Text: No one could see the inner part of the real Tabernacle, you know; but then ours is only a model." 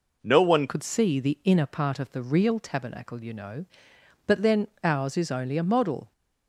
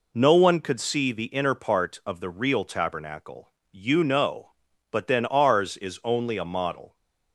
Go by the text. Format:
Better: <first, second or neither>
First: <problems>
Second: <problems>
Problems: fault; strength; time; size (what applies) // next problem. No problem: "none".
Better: second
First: changes voice at "could"; from 0.6 s on; 5.5 s long // pauses between "then" and "ours"; slight; at 4.6 s; 0.16 s long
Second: none